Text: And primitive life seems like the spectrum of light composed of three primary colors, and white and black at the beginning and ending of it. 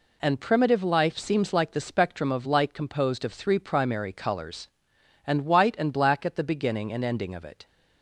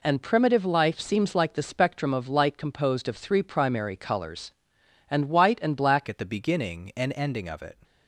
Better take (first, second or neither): first